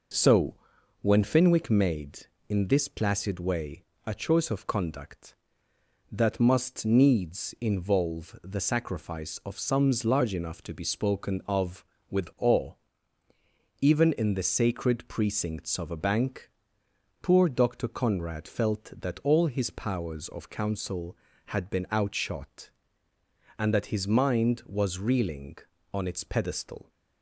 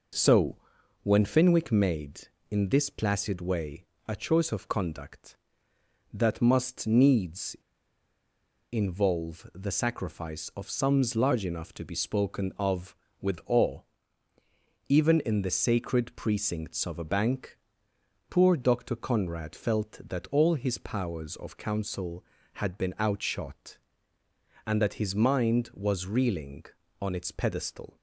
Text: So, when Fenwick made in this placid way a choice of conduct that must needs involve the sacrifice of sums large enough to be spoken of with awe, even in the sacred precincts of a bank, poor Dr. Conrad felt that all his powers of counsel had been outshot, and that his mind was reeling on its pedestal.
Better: first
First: pauses between "way" and "a"; slight; at 3.8 s; 0.20 s long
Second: pauses between "way" and "a"; slight; at 3.8 s; 0.20 s long // pauses between "needs" and "involve"; at 7.5 s; 1.1 s long

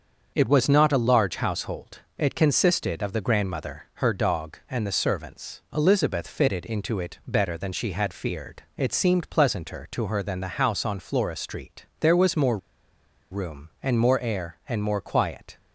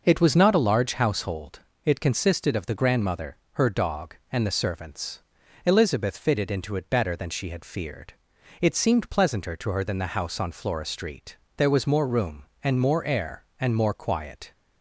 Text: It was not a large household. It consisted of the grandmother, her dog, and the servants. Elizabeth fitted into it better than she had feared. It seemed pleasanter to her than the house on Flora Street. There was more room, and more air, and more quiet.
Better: second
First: starts louder than the rest; until 1.3 s; 6.5 dB // pauses between "more" and "room"; noticeable; at 12.5 s; 0.73 s long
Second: none

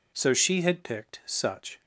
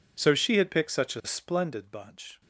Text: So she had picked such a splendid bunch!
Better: second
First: stops before "a splendid bunch"; at 1.8 s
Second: none

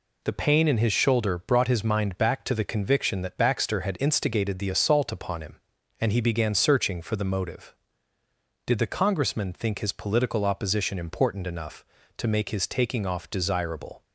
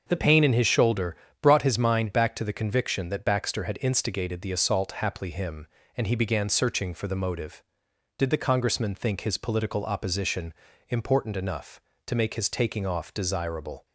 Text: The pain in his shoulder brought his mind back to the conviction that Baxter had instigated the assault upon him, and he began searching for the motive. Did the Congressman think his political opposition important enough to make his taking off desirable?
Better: first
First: none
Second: starts louder than the rest; until 1.0 s; 6.5 dB // pauses between "shoulder" and "brought"; slight; at 1.1 s; 0.26 s long // says "haply" for "upon"; at 4.9 s // pauses between "opposition" and "important"; slight; at 10.5 s; 0.36 s long

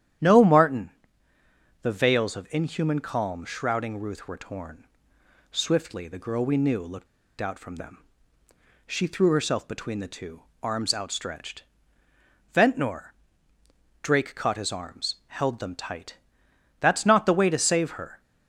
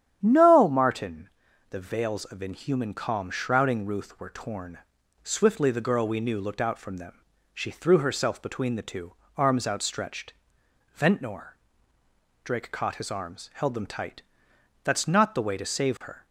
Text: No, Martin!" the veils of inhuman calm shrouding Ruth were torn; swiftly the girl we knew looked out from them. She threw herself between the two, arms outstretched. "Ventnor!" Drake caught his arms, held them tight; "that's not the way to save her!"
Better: second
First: starts louder than the rest; strong; until 2.1 s; 10.5 dB // pauses between "looked" and "out"; slight; at 7.0 s; 0.33 s long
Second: starts louder than the rest; strong; until 1.2 s; 9.5 dB

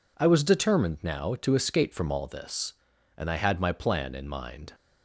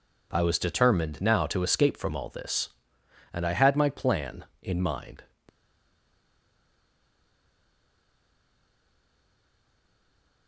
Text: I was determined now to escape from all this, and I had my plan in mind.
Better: first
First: none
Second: stays silent after the last word; strong; from 5.4 s on; 5.0 s long

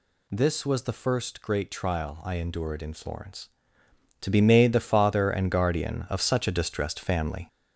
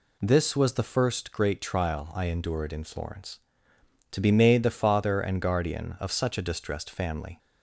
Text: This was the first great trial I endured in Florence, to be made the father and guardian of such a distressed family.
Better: second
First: gets louder; noticeable; throughout; 5.5 dB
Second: none

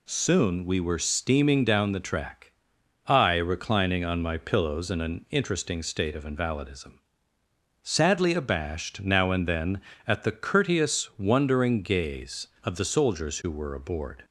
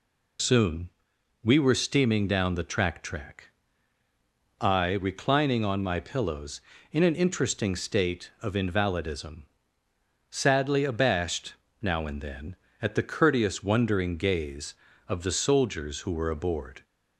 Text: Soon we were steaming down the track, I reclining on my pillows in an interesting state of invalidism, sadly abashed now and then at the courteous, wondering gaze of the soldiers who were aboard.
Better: first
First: none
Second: pauses between "Soon" and "we"; noticeable; at 0.8 s; 0.56 s long // says "track" twice; at 3.0 s // pauses between "abashed" and "now"; slight; at 11.5 s; 0.28 s long

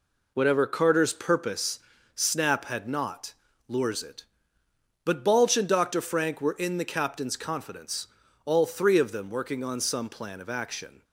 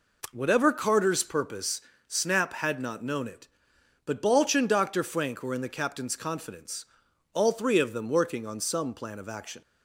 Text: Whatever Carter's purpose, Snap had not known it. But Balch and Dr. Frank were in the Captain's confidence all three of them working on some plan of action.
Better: second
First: says "lures" for "known"; at 3.6 s // pauses between "confidence" and "all"; at 8.0 s; 0.38 s long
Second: pauses between "confidence" and "all"; noticeable; at 6.8 s; 0.48 s long

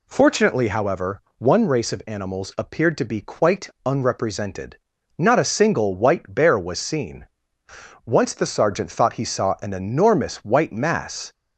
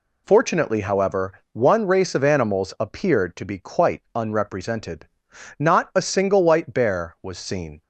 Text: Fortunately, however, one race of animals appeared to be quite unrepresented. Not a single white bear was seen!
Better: second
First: pauses between "quite" and "unrepresented"; slight; at 3.6 s; 0.16 s long // goes on to say "Once the Sergeant thought he saw an enormous white mass"; strong; from 8.0 s on; 3.2 s long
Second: none

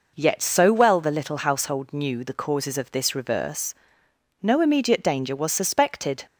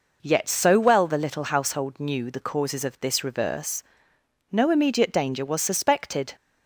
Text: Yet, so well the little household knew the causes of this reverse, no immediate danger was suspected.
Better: neither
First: none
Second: none

